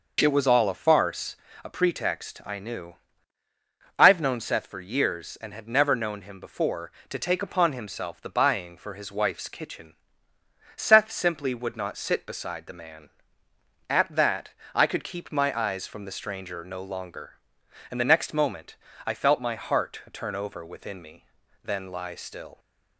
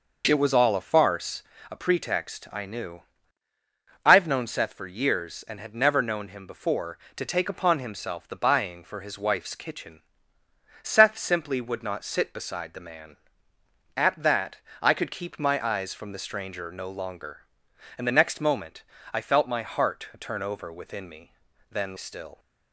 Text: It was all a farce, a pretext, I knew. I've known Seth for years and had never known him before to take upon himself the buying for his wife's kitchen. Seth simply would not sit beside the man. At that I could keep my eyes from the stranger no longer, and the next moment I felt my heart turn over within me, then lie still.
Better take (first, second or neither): first